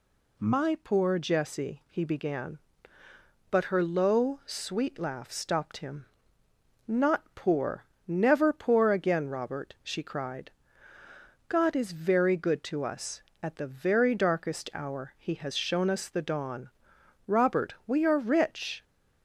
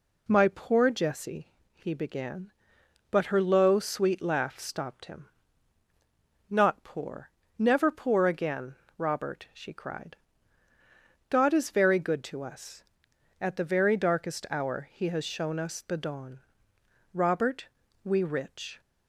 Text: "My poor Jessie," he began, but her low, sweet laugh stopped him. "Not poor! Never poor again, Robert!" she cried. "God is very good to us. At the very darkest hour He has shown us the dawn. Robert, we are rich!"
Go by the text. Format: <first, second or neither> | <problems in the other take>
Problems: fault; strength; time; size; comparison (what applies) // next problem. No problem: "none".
first | skips "are"; at 18.2 s